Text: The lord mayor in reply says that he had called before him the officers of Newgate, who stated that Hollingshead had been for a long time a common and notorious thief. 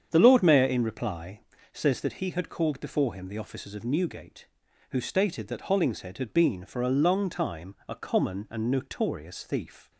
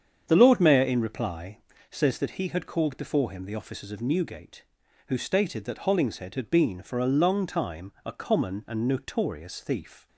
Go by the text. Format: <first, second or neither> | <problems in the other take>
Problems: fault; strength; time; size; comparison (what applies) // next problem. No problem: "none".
neither | starts louder than the rest; strong; the same in both // pauses between "reply" and "says"; slight; the same in both